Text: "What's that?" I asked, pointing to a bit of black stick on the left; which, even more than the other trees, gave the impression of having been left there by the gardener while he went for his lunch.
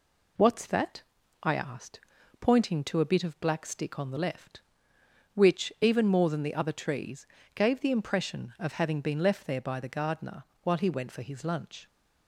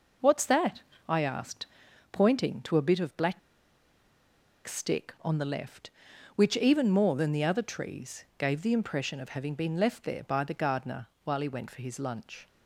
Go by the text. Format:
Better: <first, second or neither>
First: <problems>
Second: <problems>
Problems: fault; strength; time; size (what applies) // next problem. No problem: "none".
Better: first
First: pauses between "gardener" and "while"; slight; at 10.4 s; 0.22 s long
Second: pauses between "black" and "stick"; strong; at 3.3 s; 1.2 s long // pauses between "gardener" and "while"; slight; at 11.0 s; 0.16 s long